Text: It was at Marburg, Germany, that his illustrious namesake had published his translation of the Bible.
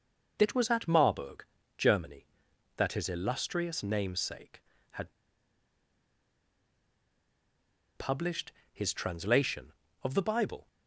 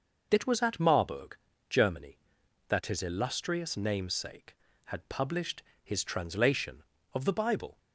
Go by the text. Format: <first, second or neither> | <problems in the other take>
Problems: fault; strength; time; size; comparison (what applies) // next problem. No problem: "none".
second | pauses between "had" and "published"; strong; at 5.1 s; 2.8 s long // pauses between "published" and "his"; slight; at 8.5 s; 0.20 s long; slight in the second